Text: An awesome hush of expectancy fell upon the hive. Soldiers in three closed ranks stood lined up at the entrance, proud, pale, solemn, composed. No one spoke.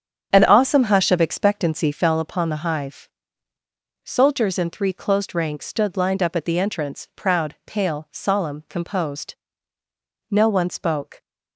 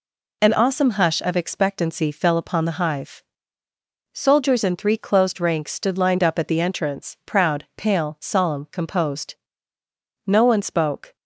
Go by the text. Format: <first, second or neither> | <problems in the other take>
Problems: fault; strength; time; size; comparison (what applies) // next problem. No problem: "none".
second | starts louder than the rest; strong; until 2.2 s; 8 dB